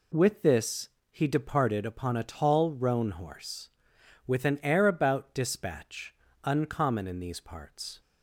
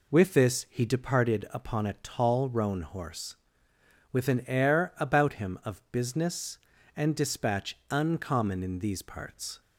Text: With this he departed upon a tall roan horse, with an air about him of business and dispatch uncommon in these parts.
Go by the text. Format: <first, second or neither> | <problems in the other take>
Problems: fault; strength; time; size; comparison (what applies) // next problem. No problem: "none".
second | pauses between "this" and "he"; slight; at 0.8 s; 0.22 s long // skips "him of business and"; at 5.3 s // pauses between "dispatch" and "uncommon"; slight; at 6.1 s; 0.30 s long